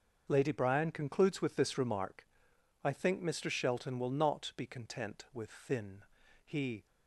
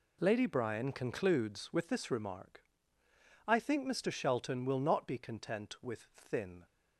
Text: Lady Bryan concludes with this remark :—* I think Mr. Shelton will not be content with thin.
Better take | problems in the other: second | starts louder than the rest; until 1.3 s; 6.5 dB // goes on to say "He"; slight; from 6.4 s on; 0.40 s long

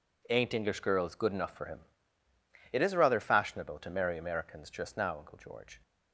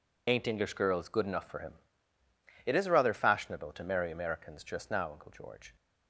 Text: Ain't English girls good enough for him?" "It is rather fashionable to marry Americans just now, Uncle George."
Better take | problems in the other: first | loses the start of "Ain't"; at 0.2 s; 90 ms

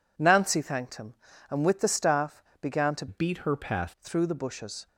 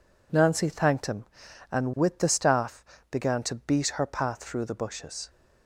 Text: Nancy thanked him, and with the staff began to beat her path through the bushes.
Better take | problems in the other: second | pauses between "staff" and "began"; slight; at 2.4 s; 0.20 s long; slight in the second // changes voice from "beat" to "path"; from 3.0 to 3.9 s; 0.9 s long

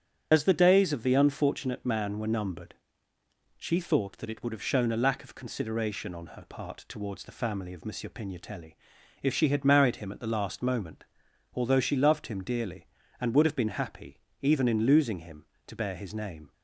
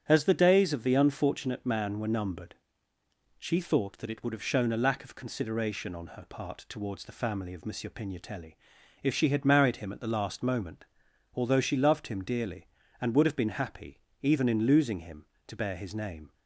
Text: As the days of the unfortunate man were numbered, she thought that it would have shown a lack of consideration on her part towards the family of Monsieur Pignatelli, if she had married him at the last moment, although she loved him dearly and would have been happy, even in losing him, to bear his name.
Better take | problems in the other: second | loses the start of "As"; at 0.3 s; 40 ms // starts louder than the rest; strong; until 1.3 s; 8.5 dB; strong in the second

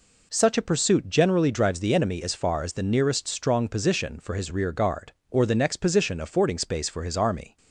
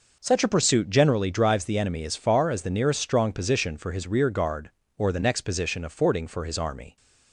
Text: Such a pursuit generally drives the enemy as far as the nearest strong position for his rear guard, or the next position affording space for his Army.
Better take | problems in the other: first | skips "space"; at 6.2 s

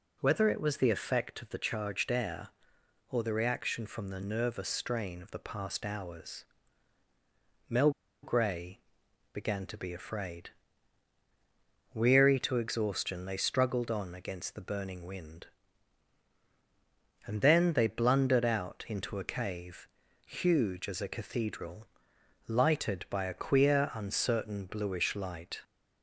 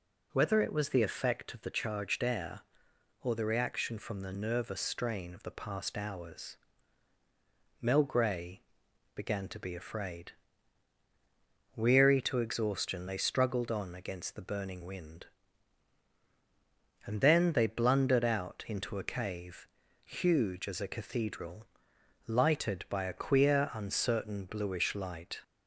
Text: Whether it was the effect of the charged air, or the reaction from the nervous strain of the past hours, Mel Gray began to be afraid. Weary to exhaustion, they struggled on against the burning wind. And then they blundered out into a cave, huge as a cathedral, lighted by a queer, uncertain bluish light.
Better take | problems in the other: second | pauses between "Mel" and "Gray"; slight; at 7.9 s; 0.32 s long // pauses between "Gray" and "began"; noticeable; at 8.7 s; 0.54 s long; noticeable in the second

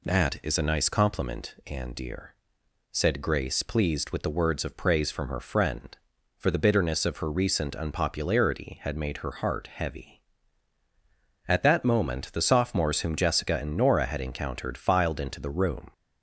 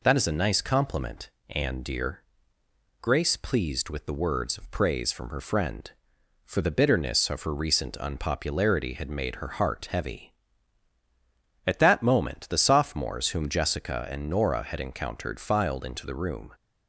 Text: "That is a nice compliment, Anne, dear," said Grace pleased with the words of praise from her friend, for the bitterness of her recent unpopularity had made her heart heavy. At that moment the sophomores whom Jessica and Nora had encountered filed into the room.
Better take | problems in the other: first | skips "said"; at 2.6 s

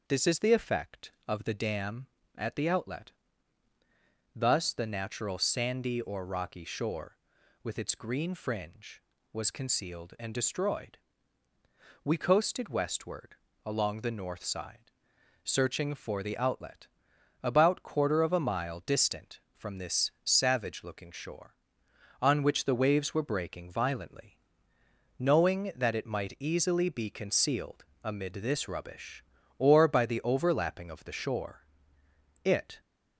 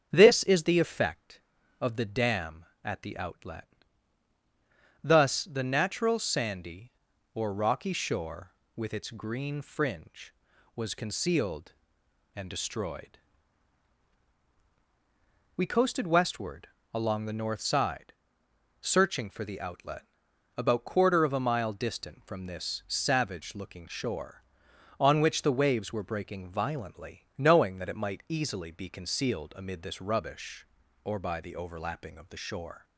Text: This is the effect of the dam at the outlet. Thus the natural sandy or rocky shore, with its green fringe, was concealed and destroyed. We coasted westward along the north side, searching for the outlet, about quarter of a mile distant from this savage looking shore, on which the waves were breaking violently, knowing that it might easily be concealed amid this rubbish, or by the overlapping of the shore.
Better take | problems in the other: second | starts louder than the rest; until 1.0 s; 6 dB; strong in the second // pauses between "westward" and "along"; slight; at 13.3 s; 0.28 s long; slight in the second // pauses between "concealed" and "amid"; slight; at 27.8 s; 0.18 s long // goes on to say "It"; slight; from 32.4 s on; 0.36 s long

